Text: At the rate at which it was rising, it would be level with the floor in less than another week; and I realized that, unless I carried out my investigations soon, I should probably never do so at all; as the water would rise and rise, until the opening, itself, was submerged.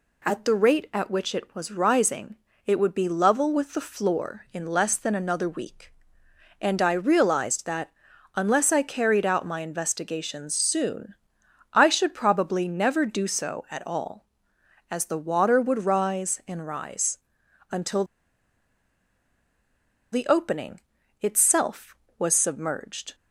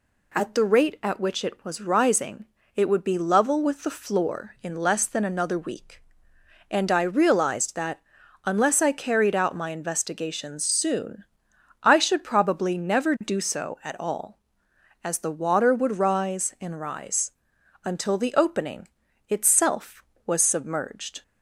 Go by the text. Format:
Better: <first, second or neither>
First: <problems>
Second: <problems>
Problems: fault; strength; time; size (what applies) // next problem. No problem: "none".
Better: second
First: pauses between "until" and "the"; strong; at 18.0 s; 2.0 s long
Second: none